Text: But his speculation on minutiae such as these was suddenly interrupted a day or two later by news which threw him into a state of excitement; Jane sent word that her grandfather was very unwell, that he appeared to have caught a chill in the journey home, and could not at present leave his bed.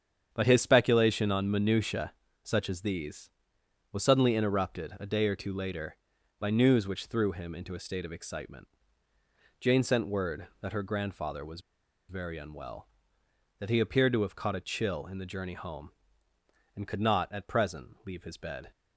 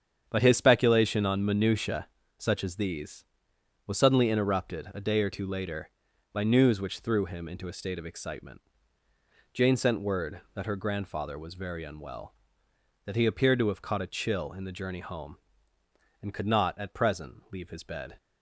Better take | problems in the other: second | starts louder than the rest; strong; until 1.3 s; 8 dB; strong in the second // pauses between "minutiae" and "such"; slight; at 2.1 s; 0.30 s long; slight in the second // pauses between "was" and "very"; noticeable; at 11.5 s; 0.49 s long

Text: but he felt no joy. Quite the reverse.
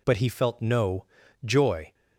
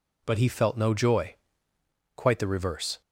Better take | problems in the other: second | pauses between "no" and "joy"; at 1.0 s; 0.40 s long // stops before "Quite the reverse"; at 1.9 s

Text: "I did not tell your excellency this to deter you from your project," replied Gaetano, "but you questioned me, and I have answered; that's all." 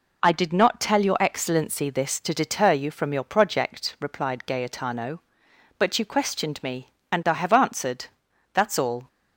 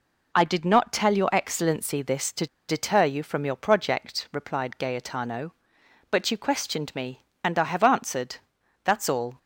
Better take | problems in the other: first | pauses between "to" and "deter"; slight; at 2.4 s; 0.22 s long

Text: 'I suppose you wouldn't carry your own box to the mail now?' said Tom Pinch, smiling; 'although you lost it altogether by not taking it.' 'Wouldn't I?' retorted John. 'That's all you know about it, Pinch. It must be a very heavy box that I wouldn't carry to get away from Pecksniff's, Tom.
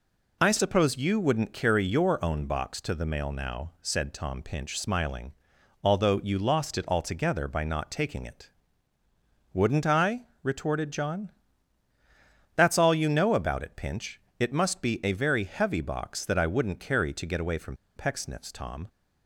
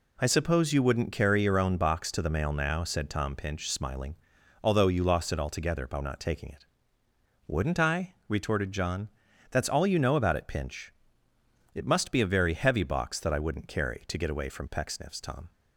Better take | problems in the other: second | pauses between "from" and "Pecksniff's"; slight; at 17.7 s; 0.21 s long

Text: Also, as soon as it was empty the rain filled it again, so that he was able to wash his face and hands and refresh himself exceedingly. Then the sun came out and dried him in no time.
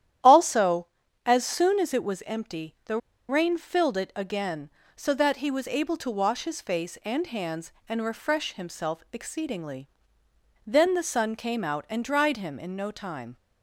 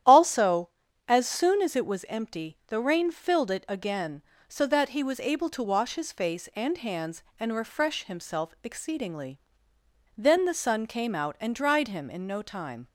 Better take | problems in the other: second | starts louder than the rest; strong; until 1.6 s; 11 dB; strong in the second // pauses between "the" and "rain"; slight; at 2.9 s; 0.31 s long

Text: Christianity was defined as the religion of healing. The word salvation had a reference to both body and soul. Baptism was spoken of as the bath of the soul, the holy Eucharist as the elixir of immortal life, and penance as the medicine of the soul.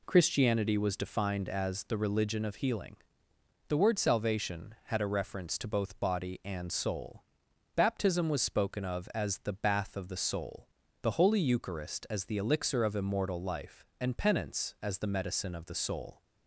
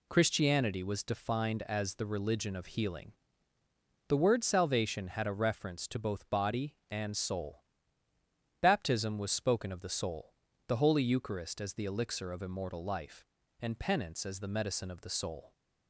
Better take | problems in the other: first | skips "as the bath of"; at 9.8 s

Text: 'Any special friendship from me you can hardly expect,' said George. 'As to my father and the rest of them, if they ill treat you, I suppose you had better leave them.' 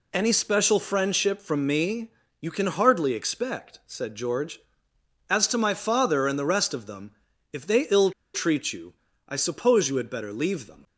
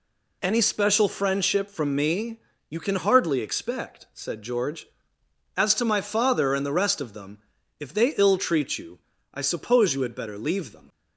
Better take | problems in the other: second | pauses between "me" and "you"; slight; at 2.1 s; 0.30 s long; slight in the second // pauses between "ill" and "treat"; slight; at 8.1 s; 0.23 s long

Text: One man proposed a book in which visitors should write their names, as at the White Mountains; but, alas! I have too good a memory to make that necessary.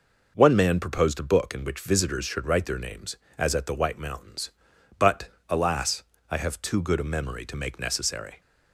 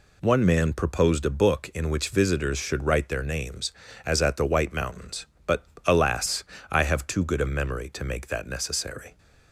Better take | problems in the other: second | skips "that"; at 7.7 s

